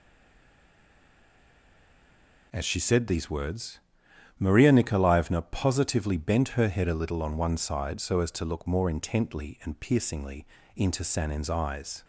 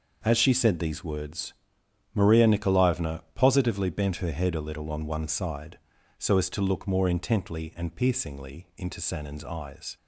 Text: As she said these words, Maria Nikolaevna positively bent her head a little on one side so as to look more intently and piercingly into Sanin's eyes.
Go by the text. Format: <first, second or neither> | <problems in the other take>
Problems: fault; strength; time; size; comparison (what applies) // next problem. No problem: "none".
second | stays silent before the first word; until 2.5 s; 2.5 s long // pauses between "piercingly" and "into"; slight; at 10.4 s; 0.30 s long